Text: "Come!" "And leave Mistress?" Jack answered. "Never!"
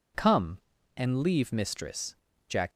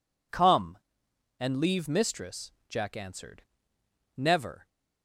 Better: second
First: stops before "answered Never"; at 2.7 s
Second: none

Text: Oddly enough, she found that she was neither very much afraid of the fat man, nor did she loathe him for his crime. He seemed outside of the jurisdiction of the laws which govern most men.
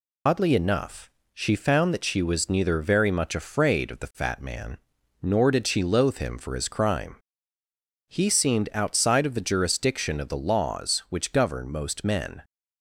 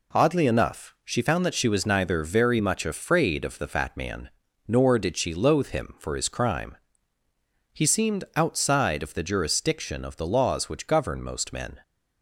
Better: second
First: loses the start of "Oddly"; at 0.2 s; 95 ms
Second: none

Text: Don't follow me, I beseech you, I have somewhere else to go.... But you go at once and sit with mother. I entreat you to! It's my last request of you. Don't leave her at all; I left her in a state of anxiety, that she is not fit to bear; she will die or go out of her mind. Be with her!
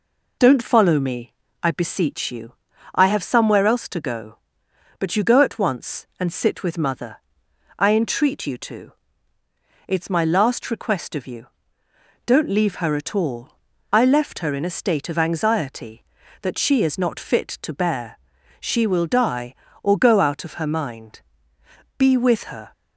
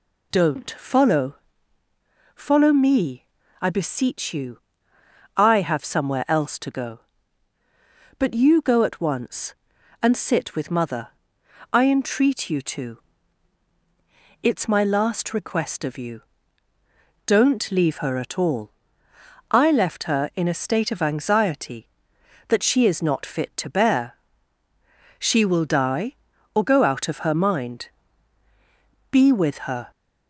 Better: first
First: none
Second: says "follow" twice; at 2.3 s

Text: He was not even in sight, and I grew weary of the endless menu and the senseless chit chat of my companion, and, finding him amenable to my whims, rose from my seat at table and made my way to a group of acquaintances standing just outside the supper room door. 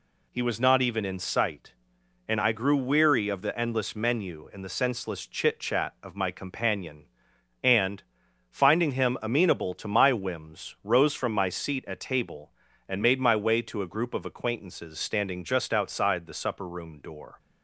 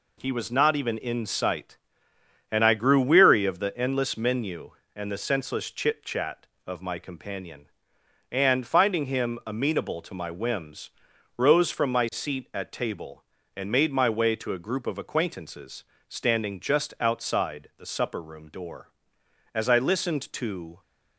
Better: first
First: none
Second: pauses between "acquaintances" and "standing"; slight; at 15.8 s; 0.24 s long // goes on to say "As I listened to"; noticeable; from 19.5 s on; 1.2 s long

